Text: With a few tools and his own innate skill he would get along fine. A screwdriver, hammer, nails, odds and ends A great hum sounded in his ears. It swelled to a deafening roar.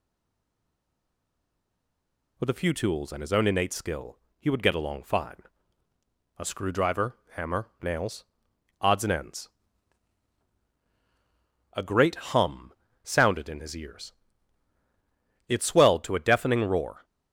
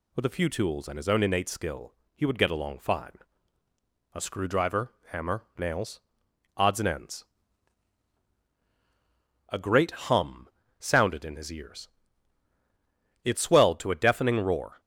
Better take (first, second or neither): second